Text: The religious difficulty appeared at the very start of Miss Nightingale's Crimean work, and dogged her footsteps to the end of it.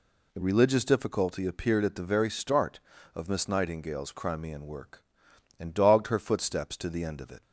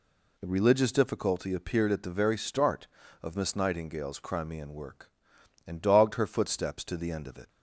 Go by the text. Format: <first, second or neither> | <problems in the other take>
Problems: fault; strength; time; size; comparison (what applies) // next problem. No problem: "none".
neither | none